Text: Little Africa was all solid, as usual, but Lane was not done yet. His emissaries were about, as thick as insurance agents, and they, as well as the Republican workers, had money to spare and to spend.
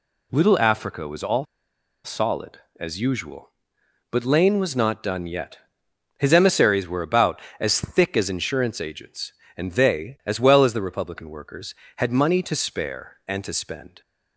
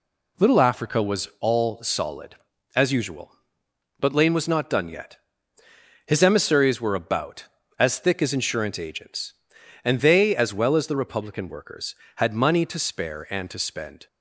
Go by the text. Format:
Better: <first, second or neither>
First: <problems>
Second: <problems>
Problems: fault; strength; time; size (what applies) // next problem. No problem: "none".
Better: second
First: pauses between "all" and "solid"; noticeable; at 1.4 s; 0.60 s long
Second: none